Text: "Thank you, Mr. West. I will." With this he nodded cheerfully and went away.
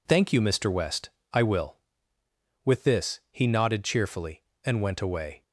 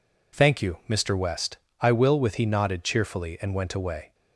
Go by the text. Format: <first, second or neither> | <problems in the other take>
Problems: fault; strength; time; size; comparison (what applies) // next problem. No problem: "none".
first | skips "this"; at 2.4 s